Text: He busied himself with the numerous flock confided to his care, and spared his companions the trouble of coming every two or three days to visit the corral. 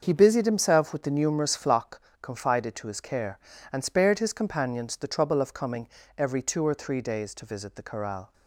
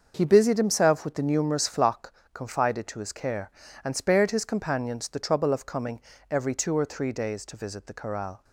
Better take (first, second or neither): neither